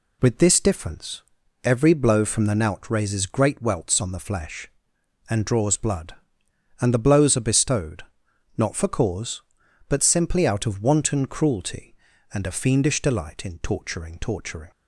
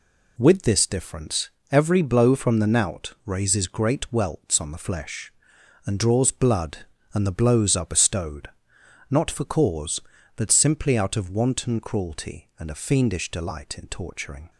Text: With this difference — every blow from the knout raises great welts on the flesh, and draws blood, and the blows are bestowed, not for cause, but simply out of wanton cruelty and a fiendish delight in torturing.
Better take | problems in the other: second | says "torturing" twice; at 14.1 s

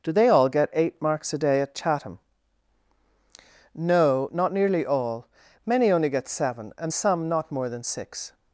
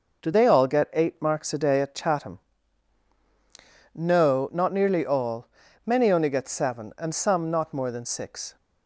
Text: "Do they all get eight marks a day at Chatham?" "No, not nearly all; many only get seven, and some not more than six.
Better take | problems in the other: neither | none

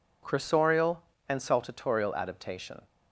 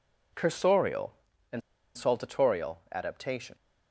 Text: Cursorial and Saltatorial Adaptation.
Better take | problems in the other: first | pauses between "and" and "Saltatorial"; slight; at 1.6 s; 0.36 s long

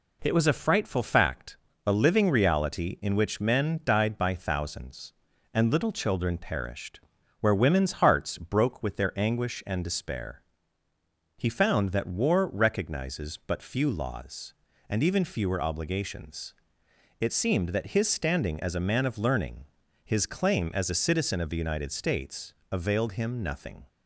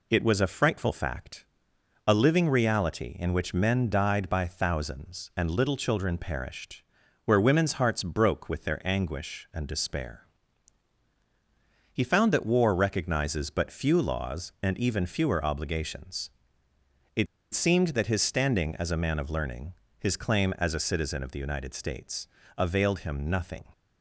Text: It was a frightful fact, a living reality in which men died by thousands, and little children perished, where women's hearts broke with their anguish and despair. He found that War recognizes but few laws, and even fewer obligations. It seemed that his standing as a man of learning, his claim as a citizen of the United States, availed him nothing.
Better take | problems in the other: first | pauses between "It" and "seemed"; slight; at 17.2 s; 0.27 s long

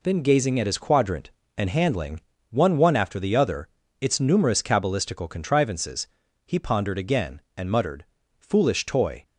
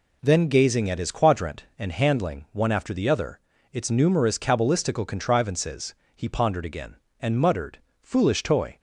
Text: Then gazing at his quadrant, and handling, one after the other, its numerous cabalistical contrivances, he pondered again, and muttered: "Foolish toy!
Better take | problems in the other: second | says "one" twice; at 2.7 s

